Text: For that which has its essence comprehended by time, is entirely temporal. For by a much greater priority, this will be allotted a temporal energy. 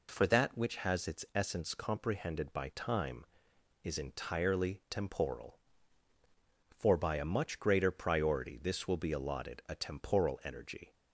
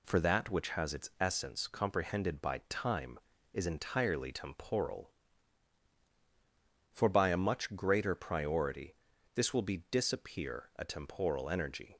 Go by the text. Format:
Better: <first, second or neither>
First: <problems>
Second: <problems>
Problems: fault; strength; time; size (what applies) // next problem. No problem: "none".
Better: first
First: none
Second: says "disappear" for "allotted"; at 9.9 s